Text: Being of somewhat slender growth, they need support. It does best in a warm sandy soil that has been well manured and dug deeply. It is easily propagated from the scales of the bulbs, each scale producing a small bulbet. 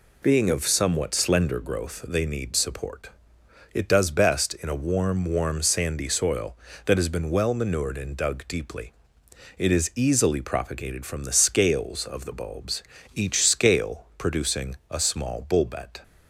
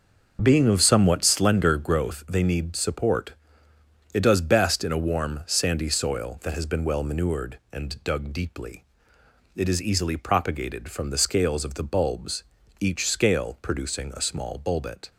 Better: second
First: says "warm" twice; at 5.2 s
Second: none

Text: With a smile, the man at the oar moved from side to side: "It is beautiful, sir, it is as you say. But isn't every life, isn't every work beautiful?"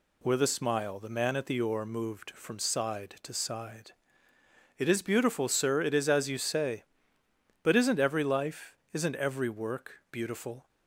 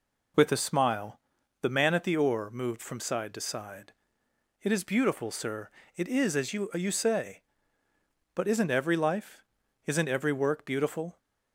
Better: first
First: none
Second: says "you" twice; at 6.7 s

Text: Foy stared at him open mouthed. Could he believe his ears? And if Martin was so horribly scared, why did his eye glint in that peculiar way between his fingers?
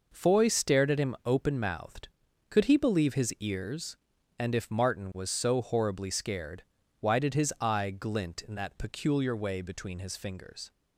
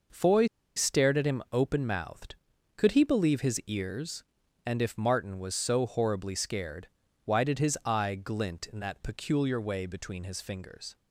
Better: first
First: none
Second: pauses between "Foy" and "stared"; slight; at 0.4 s; 0.31 s long

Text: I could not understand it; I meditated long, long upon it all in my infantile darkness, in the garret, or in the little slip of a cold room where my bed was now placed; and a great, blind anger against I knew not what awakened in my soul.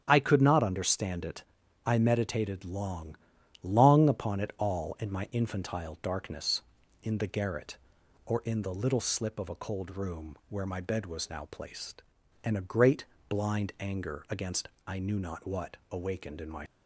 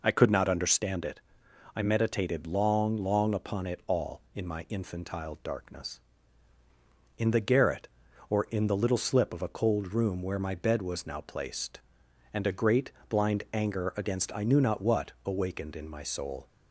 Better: second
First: starts louder than the rest; strong; until 1.0 s; 8.5 dB // pauses between "against" and "I"; slight; at 14.6 s; 0.22 s long // stops before "soul"; at 16.6 s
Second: none

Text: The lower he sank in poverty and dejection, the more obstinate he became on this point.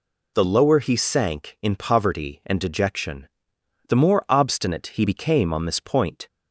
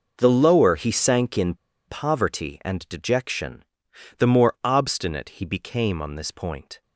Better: first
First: none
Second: pauses between "in" and "poverty"; slight; at 1.5 s; 0.33 s long

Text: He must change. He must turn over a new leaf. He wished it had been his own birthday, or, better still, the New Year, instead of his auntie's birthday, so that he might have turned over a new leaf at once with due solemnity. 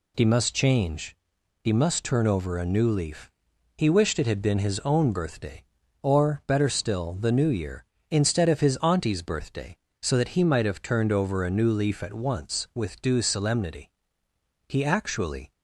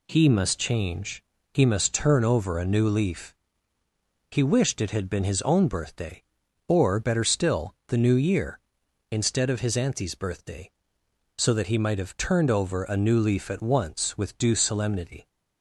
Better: second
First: goes on to say "He actually"; noticeable; from 14.6 s on; 0.82 s long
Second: none

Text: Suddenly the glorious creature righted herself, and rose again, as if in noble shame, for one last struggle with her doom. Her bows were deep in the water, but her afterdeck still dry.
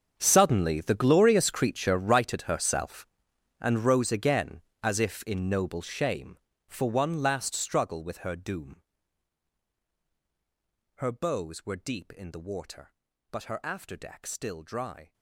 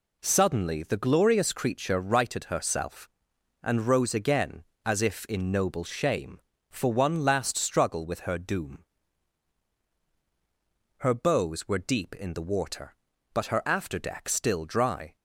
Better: second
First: gets quieter; strong; throughout; 18.5 dB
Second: none

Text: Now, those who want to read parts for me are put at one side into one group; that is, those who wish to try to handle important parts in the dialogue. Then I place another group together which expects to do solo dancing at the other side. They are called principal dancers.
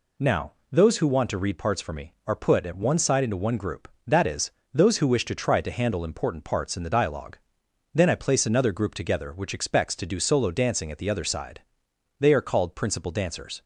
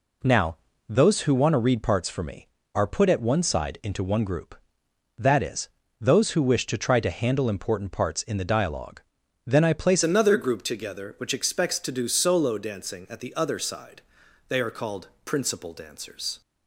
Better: first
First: none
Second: changes voice at "another"; from 10.0 s on; 6.4 s long // pauses between "called" and "principal"; slight; at 15.0 s; 0.16 s long

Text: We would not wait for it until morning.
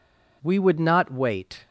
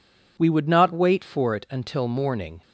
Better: second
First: stops before "for it until morning"; at 1.6 s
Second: none

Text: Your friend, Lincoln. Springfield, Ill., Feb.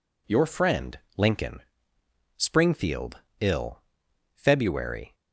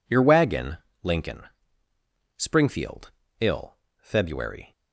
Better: first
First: none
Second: says "wagon" for "friend"; at 0.2 s

